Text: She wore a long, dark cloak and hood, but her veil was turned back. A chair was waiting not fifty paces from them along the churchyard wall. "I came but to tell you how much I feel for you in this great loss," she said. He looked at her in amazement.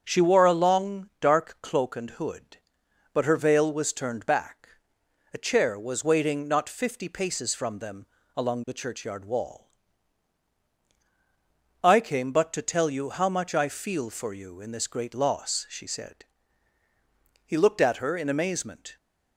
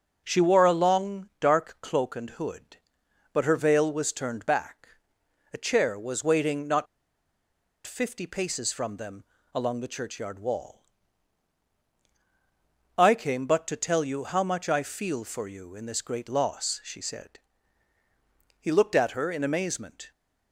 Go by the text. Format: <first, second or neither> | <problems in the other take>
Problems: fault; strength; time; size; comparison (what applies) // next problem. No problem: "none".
first | pauses between "not" and "fifty"; at 6.8 s; 1.0 s long // pauses between "them" and "along"; slight; at 9.2 s; 0.32 s long; slight in the first